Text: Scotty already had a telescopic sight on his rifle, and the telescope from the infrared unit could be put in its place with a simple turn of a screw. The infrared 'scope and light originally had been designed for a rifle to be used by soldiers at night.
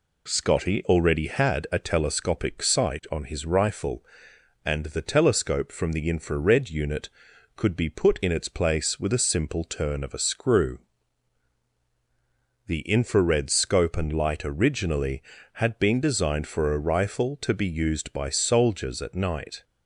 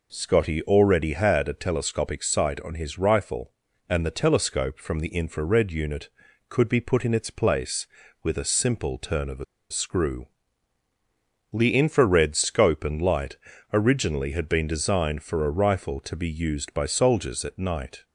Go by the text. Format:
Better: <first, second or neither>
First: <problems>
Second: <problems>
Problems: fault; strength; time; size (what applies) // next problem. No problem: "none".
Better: first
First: none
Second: pauses between "a" and "screw"; slight; at 9.4 s; 0.25 s long // pauses between "light" and "originally"; slight; at 13.3 s; 0.34 s long